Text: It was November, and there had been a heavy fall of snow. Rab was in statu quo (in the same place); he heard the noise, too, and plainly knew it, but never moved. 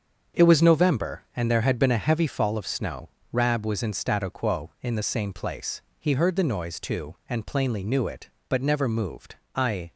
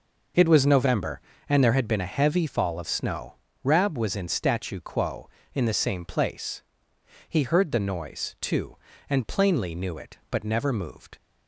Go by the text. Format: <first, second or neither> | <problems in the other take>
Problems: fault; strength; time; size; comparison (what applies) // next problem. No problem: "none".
second | starts louder than the rest; until 1.4 s; 7 dB // goes on to say "I"; slight; from 9.5 s on; 0.38 s long